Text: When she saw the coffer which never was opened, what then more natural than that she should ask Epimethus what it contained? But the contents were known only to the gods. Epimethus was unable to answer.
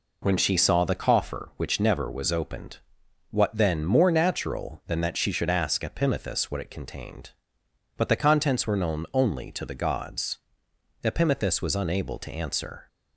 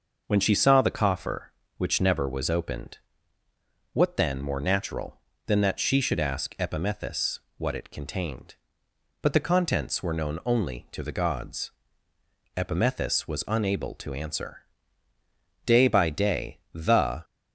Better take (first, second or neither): first